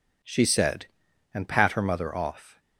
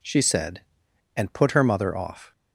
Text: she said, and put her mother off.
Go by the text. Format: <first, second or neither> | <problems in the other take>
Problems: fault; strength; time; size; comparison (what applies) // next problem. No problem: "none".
second | says "pat" for "put"; at 1.4 s